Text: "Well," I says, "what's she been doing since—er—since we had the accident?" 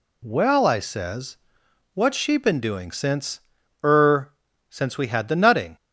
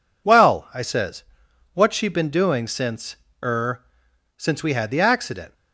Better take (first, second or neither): second